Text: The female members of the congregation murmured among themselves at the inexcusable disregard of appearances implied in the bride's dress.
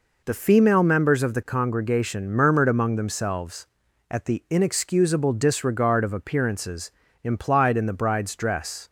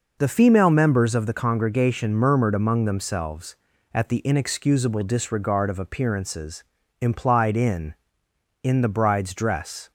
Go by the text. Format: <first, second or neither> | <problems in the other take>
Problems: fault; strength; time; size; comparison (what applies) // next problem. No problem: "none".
first | pauses between "appearances" and "implied"; at 6.6 s; 0.40 s long; slight in the first // says "in" twice; at 8.6 s